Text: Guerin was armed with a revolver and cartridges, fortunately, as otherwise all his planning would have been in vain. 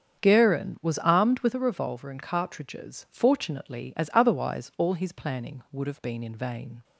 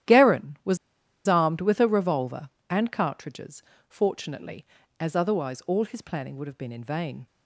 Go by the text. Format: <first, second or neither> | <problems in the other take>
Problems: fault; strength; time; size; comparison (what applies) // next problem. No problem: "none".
first | starts louder than the rest; strong; until 1.6 s; 12 dB; strong in the first // pauses between "was" and "armed"; noticeable; at 0.7 s; 0.50 s long